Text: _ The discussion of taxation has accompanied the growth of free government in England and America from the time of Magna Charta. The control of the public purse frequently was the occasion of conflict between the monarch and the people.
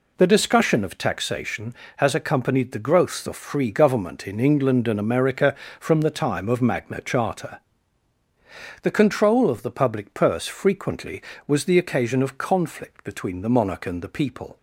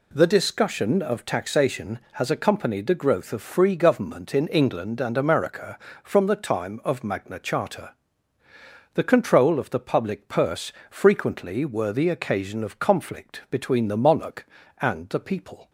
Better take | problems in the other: first | pauses between "purse" and "frequently"; slight; at 10.6 s; 0.20 s long // says "were" for "was"; at 11.6 s

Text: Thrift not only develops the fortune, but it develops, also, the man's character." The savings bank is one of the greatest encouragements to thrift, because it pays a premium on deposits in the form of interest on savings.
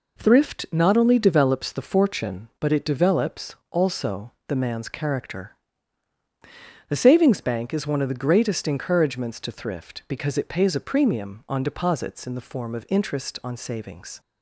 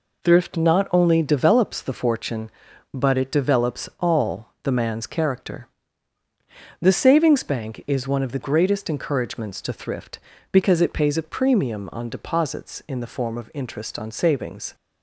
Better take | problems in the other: first | says "all" for "also"; at 3.9 s

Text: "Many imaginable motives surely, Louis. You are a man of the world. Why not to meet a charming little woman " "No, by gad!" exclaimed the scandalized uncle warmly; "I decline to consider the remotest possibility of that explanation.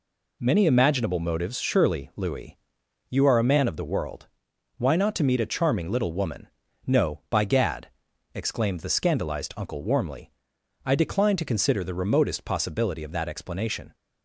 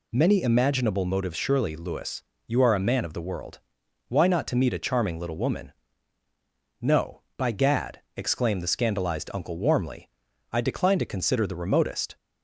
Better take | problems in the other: first | stops before "possibility of that explanation"; at 12.1 s

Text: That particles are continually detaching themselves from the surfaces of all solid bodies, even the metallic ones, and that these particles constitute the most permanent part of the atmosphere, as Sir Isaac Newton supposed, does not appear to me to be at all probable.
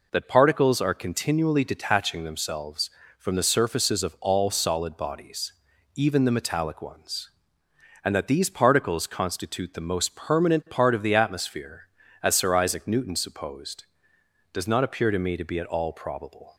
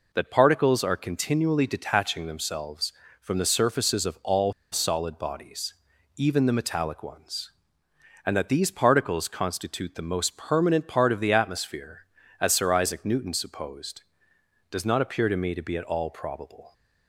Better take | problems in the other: first | pauses between "all" and "solid"; slight; at 4.5 s; 0.19 s long

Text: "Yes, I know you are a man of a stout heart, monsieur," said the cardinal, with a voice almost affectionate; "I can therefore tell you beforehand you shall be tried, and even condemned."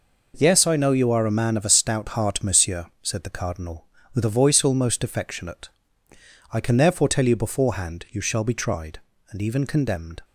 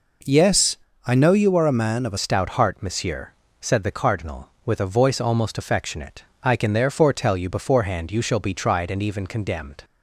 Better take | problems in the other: first | changes voice at "stout"; from 2.1 s on; 7.7 s long

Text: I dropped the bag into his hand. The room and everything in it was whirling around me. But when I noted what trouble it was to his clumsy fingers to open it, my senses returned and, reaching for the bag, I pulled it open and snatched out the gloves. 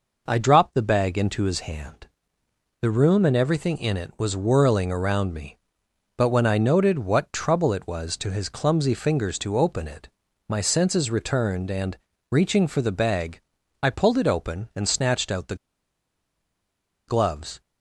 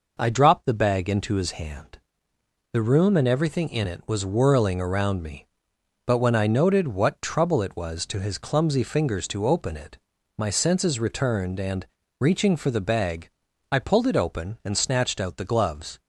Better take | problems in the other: second | pauses between "the" and "gloves"; strong; at 15.5 s; 1.5 s long

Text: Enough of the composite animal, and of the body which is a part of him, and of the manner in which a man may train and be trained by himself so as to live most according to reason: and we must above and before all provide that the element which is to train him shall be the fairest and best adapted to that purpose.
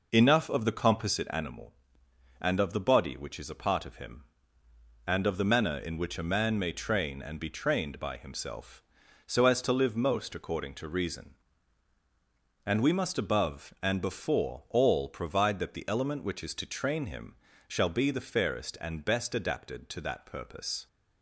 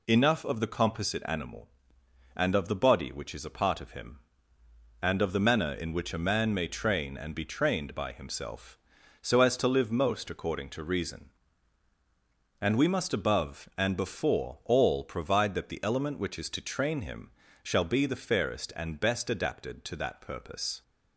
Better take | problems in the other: second | starts louder than the rest; noticeable; until 1.4 s; 5 dB // pauses between "him" and "shall"; slight; at 17.3 s; 0.32 s long; slight in the second

